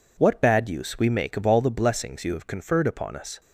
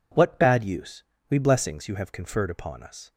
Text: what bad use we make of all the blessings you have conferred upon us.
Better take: first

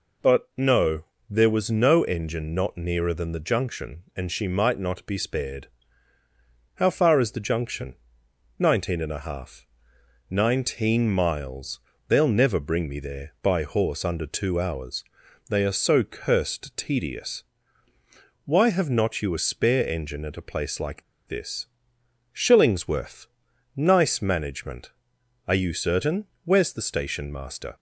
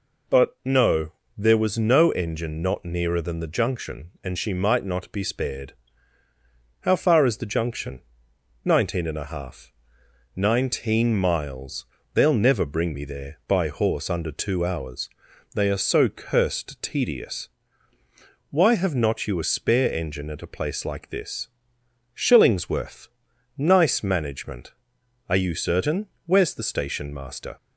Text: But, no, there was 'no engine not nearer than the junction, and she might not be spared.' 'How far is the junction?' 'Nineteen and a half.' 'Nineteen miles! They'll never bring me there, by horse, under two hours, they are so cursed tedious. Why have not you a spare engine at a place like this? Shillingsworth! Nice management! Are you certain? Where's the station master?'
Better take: second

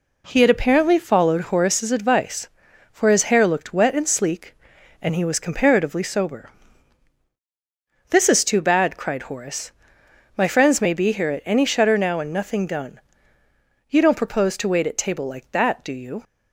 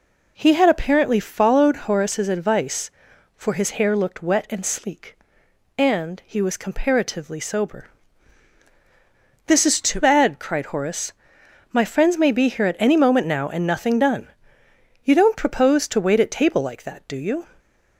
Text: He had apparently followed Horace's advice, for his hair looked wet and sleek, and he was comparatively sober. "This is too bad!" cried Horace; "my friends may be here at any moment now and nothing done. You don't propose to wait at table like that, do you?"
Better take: second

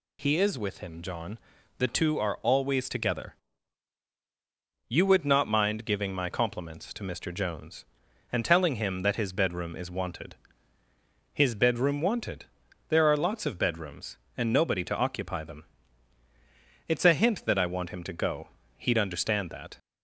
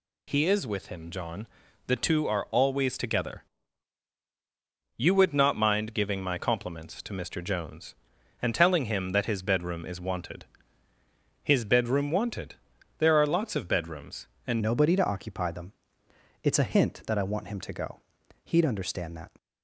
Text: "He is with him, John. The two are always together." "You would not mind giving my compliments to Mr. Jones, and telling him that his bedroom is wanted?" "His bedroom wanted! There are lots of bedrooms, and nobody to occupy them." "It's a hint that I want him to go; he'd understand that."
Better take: first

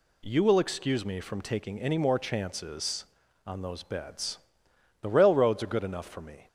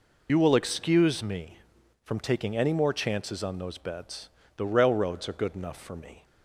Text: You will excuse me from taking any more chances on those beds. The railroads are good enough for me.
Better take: first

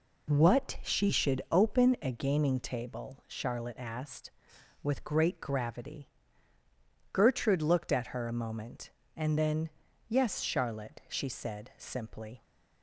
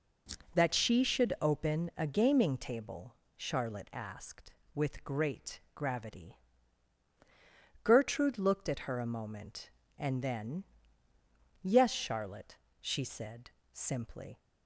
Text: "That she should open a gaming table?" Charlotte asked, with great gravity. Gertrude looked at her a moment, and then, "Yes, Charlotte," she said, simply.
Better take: second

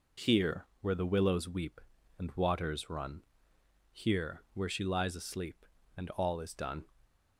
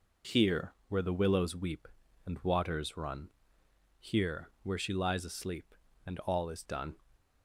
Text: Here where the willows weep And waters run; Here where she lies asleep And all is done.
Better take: neither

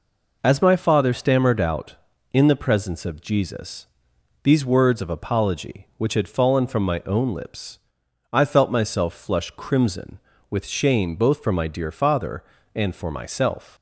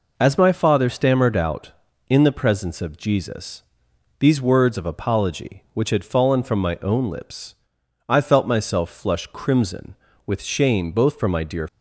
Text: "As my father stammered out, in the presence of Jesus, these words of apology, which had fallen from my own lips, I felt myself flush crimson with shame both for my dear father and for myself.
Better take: first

